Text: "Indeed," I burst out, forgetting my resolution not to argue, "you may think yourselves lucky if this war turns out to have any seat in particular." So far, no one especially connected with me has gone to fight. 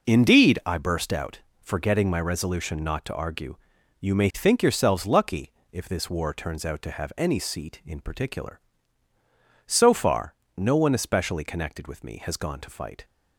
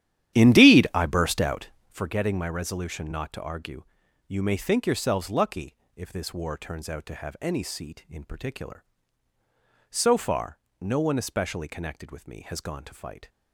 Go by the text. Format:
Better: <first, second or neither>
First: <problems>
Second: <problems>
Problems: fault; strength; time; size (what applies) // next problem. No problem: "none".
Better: first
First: pauses between "lucky" and "if"; slight; at 5.5 s; 0.18 s long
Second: starts louder than the rest; strong; until 2.0 s; 11.5 dB // pauses between "lucky" and "if"; slight; at 5.7 s; 0.18 s long